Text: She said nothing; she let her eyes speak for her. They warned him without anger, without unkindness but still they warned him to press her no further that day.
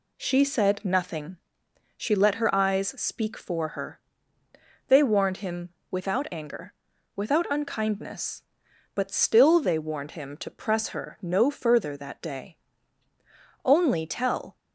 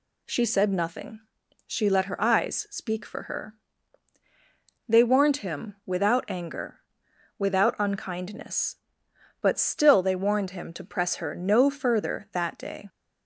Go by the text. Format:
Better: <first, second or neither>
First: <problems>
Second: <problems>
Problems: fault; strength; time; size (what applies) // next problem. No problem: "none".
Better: second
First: pauses between "him" and "without"; slight; at 5.6 s; 0.22 s long // goes on to say "Only tell"; noticeable; from 13.6 s on; 0.90 s long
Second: none